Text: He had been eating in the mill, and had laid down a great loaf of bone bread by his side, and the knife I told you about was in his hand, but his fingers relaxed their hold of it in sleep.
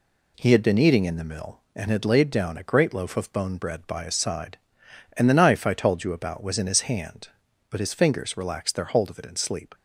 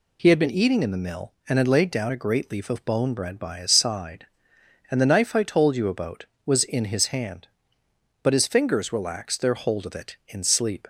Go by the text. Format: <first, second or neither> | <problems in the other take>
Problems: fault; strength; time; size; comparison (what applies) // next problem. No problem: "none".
first | says "leaf" for "loaf"; at 2.5 s